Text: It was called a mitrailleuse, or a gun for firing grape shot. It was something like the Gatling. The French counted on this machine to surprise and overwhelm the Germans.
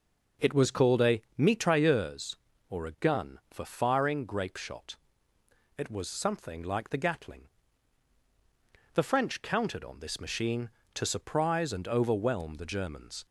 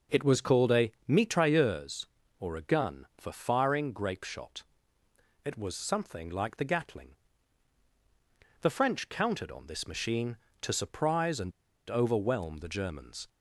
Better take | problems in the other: first | pauses between "a" and "mitrailleuse"; slight; at 0.9 s; 0.18 s long; slight in the first // pauses between "and" and "overwhelm"; at 11.5 s; 0.38 s long

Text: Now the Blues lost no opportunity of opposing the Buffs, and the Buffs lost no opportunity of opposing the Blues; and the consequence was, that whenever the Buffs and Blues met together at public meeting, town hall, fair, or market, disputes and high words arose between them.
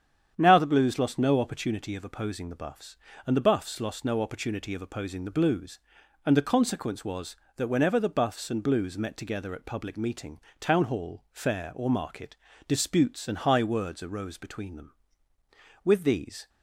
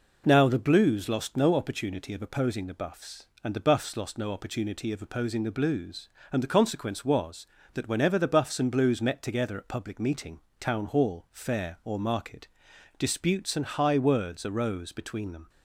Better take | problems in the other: second | starts louder than the rest; strong; until 1.3 s; 8.5 dB // goes on to say "With these"; noticeable; from 15.8 s on; 0.64 s long

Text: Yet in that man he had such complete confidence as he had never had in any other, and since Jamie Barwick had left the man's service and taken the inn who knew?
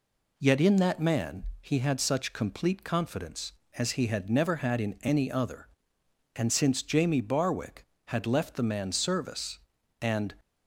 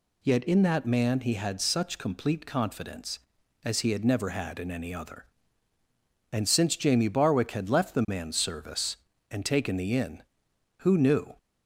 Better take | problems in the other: second | pauses between "man" and "he"; slight; at 1.4 s; 0.16 s long // stops before "taken the inn who knew"; at 10.4 s

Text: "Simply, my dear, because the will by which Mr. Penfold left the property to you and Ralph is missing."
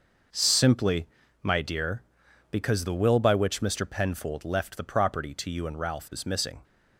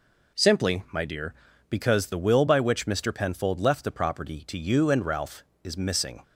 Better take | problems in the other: neither | none

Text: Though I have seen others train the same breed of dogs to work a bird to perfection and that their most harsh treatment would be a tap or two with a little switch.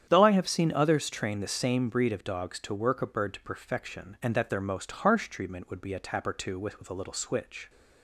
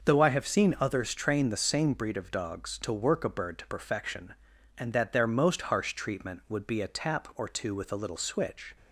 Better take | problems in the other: second | starts louder than the rest; strong; until 1.1 s; 9 dB; noticeable in the second // says "with" twice; at 6.7 s

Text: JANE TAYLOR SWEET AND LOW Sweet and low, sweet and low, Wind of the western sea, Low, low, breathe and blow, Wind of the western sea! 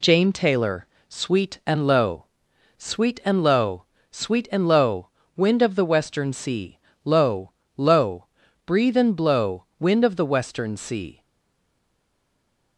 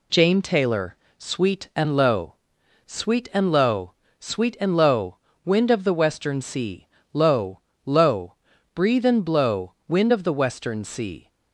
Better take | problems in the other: second | pauses between "TAYLOR" and "SWEET"; slight; at 0.8 s; 0.22 s long; slight in the second // pauses between "LOW" and "Sweet"; noticeable; at 2.2 s; 0.50 s long; noticeable in the second // stays silent after the last word; noticeable; from 11.2 s on; 1.5 s long

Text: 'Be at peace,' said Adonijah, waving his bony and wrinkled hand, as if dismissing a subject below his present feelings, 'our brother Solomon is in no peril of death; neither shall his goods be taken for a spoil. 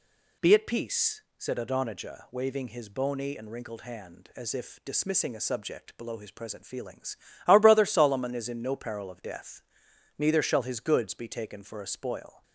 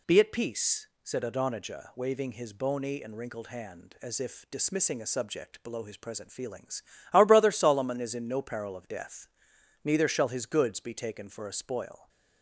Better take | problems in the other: neither | none

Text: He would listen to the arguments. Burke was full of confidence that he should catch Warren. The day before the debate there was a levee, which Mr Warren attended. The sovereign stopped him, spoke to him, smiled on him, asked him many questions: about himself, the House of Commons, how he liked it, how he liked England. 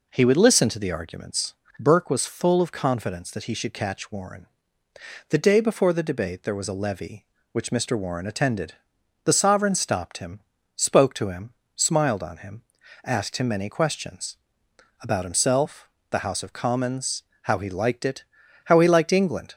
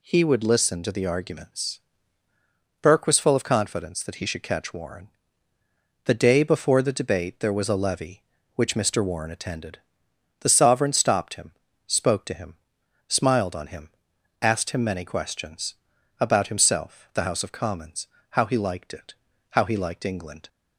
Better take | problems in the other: neither | none

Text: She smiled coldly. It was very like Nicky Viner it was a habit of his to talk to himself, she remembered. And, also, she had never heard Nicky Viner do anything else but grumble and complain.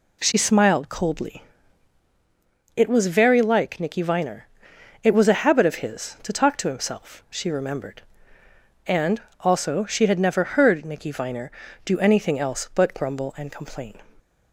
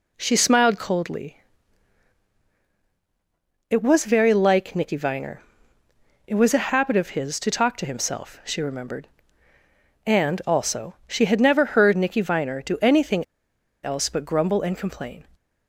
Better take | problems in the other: first | pauses between "Viner" and "it"; noticeable; at 5.4 s; 0.86 s long; noticeable in the first // pauses between "anything" and "else"; noticeable; at 13.2 s; 0.59 s long

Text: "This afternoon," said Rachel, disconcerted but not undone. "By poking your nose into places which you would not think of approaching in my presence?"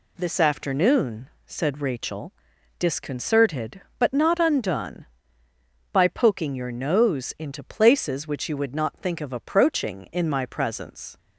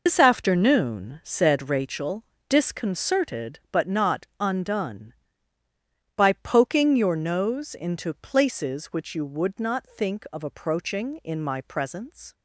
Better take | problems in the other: first | loses the start of "This"; at 0.0 s; 125 ms

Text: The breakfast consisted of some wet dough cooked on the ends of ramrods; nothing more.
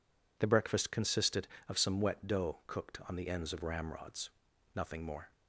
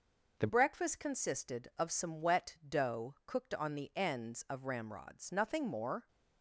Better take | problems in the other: first | changes voice at "breakfast"; from 0.4 s on; 5.6 s long

